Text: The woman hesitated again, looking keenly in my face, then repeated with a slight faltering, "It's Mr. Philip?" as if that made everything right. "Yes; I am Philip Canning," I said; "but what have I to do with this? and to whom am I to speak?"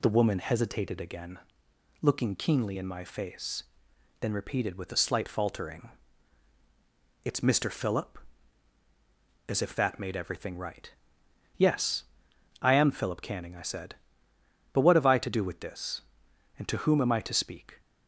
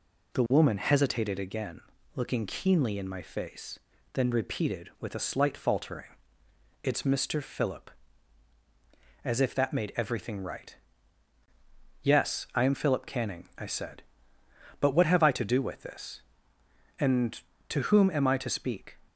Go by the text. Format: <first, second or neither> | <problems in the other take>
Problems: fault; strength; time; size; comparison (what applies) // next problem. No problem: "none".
neither | none